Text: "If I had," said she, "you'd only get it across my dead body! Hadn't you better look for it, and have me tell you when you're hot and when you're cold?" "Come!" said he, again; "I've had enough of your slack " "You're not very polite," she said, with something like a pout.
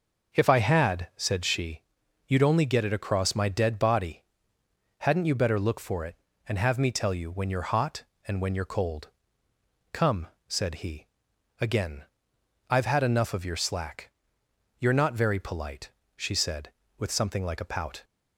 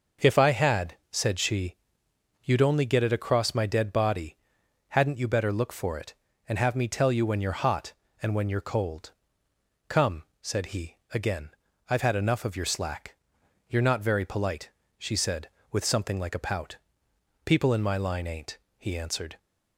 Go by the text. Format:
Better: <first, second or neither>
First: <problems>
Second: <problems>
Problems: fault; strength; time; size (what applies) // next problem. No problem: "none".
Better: first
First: none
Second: goes on to say "People in my line ain't he answered"; strong; from 17.4 s on; 1.9 s long